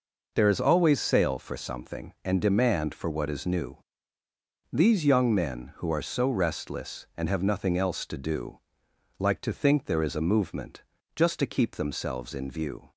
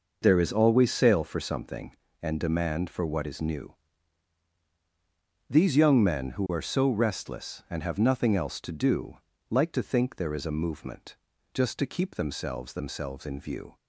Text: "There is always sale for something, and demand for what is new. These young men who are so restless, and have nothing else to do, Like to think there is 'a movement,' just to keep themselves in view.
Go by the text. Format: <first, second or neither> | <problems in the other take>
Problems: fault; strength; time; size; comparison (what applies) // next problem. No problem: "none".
first | says "themselves" twice; at 12.7 s